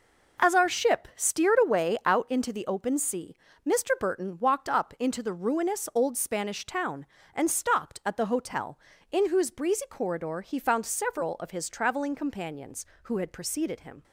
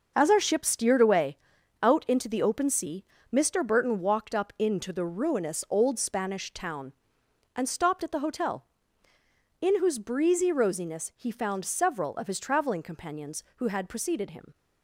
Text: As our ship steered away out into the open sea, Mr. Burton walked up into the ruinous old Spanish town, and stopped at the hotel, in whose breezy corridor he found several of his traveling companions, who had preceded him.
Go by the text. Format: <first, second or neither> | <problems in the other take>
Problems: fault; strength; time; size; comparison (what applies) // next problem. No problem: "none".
first | pauses between "away" and "out"; noticeable; at 1.3 s; 0.46 s long // says "rosiness" for "corridor"; at 10.5 s